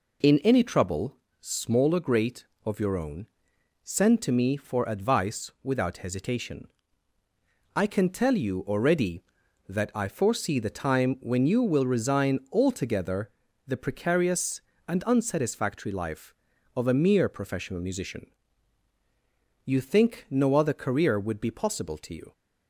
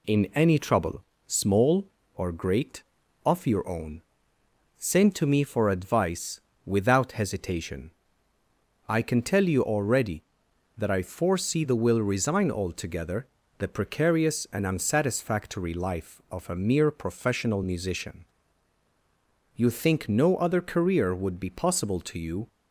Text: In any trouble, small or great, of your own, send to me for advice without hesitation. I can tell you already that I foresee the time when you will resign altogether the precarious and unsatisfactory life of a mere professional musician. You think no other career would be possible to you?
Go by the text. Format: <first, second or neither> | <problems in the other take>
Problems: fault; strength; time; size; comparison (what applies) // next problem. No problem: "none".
first | pauses between "advice" and "without"; slight; at 6.4 s; 0.26 s long // skips "time when you"; at 11.7 s // pauses between "altogether" and "the"; slight; at 13.2 s; 0.32 s long; slight in the first